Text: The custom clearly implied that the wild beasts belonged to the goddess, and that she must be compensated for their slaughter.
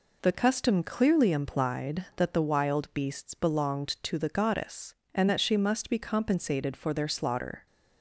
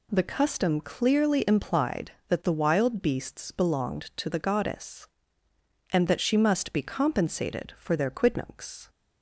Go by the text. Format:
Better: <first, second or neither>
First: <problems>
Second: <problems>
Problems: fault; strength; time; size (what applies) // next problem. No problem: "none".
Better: first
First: none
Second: says "quidnuncs" for "slaughter"; at 8.1 s